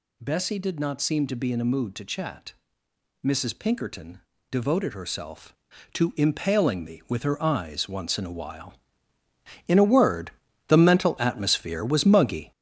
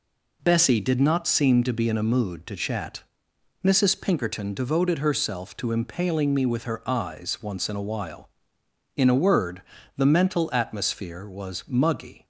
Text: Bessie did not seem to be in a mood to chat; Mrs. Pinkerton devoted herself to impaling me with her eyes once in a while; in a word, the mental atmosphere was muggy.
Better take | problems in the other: second | gets louder; throughout; 7 dB // pauses between "Pinkerton" and "devoted"; slight; at 4.2 s; 0.28 s long

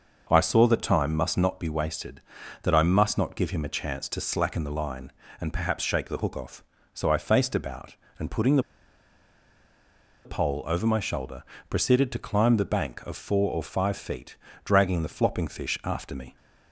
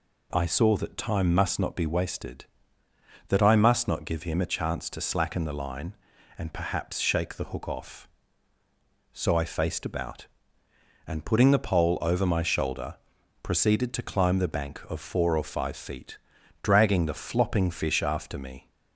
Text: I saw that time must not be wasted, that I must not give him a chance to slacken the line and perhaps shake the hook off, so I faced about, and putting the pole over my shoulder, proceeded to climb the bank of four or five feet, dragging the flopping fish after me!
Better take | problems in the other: second | pauses between "the" and "pole"; strong; at 8.6 s; 1.6 s long

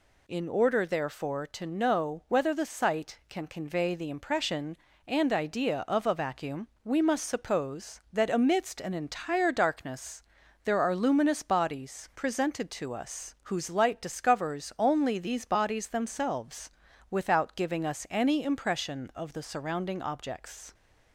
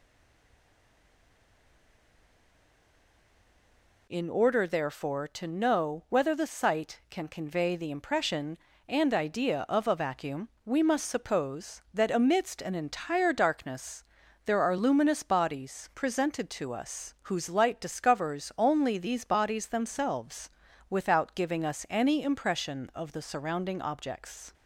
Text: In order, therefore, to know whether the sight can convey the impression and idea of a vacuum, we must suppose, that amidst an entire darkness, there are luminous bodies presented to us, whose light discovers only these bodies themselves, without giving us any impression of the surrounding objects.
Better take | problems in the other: first | stays silent before the first word; strong; until 4.0 s; 4.0 s long

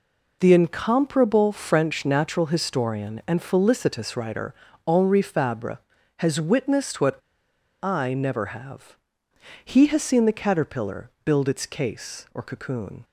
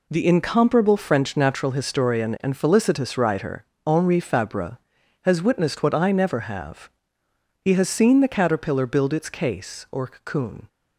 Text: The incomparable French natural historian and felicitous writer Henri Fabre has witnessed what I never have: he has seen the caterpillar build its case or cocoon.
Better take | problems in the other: second | pauses between "writer" and "Henri"; slight; at 4.5 s; 0.32 s long; slight in the second // pauses between "what" and "I"; noticeable; at 7.1 s; 0.67 s long // pauses between "caterpillar" and "build"; slight; at 11.1 s; 0.16 s long

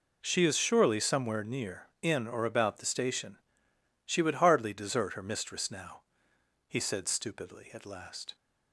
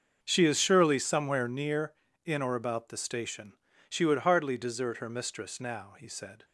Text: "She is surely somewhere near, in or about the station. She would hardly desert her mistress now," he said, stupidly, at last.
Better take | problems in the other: first | starts louder than the rest; until 1.2 s; 6 dB // stops before "stupidly at last"; at 6.4 s

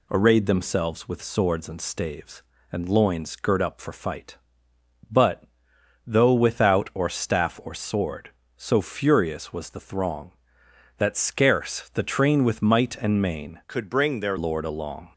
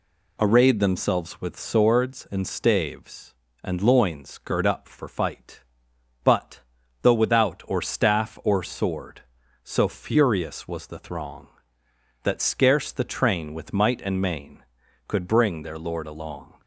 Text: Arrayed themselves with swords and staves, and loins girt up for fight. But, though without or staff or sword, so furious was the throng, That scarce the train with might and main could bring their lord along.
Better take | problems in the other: second | changes voice from "could" to "their"; from 13.6 to 14.3 s; 0.7 s long

